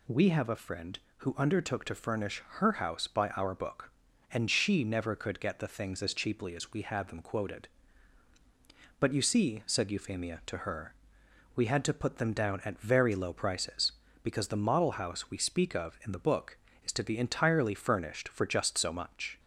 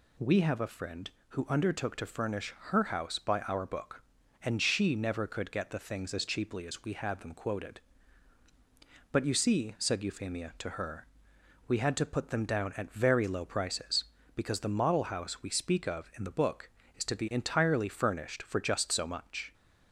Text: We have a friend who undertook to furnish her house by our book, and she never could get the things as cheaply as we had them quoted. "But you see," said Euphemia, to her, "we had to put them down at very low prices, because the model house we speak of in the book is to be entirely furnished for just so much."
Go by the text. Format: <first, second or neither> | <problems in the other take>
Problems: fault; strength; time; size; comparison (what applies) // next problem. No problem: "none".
neither | pauses between "furnish" and "her"; slight; the same in both